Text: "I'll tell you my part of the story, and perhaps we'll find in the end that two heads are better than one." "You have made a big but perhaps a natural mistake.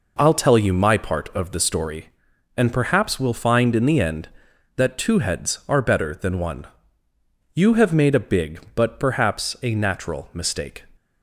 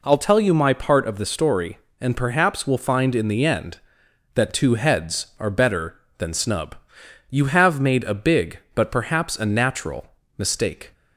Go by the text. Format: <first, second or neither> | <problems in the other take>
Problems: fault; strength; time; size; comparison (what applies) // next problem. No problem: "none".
first | says "snub" for "one"; at 6.3 s // pauses between "natural" and "mistake"; slight; at 10.0 s; 0.28 s long